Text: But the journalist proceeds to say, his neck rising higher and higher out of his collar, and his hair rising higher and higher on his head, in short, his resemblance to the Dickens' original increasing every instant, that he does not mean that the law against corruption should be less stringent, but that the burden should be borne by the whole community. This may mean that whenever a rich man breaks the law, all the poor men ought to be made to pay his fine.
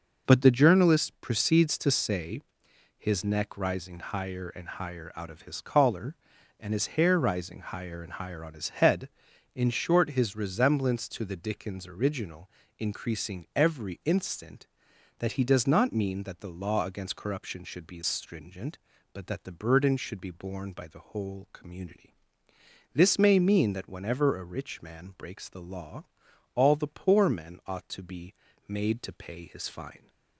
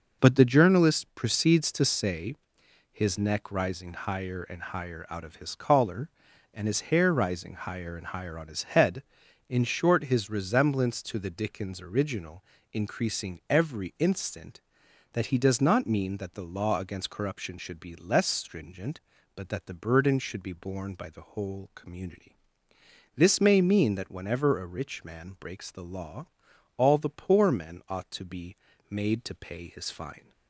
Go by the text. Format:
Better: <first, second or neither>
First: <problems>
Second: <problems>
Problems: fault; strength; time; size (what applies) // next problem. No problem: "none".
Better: second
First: pauses between "original" and "increasing"; slight; at 12.5 s; 0.28 s long // skips "less"; at 18.0 s // pauses between "be" and "made"; slight; at 28.3 s; 0.34 s long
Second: pauses between "original" and "increasing"; slight; at 12.4 s; 0.28 s long // pauses between "be" and "made"; slight; at 28.5 s; 0.34 s long